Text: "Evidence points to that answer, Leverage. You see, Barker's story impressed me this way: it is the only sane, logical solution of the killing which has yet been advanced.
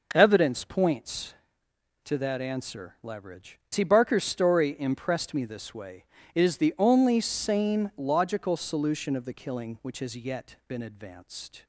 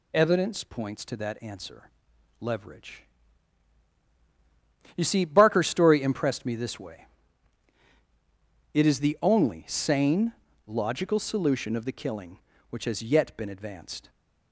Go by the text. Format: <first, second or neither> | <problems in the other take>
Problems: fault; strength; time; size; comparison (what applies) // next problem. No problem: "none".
second | skips "You"; at 3.6 s